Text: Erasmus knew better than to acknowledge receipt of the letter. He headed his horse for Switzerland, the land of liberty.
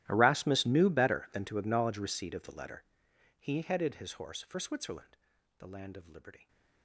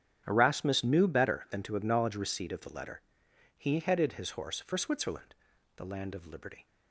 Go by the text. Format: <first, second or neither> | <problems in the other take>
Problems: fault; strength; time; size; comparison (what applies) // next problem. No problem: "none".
second | gets quieter; strong; throughout; 24 dB // starts louder than the rest; strong; until 1.1 s; 14 dB; strong in the second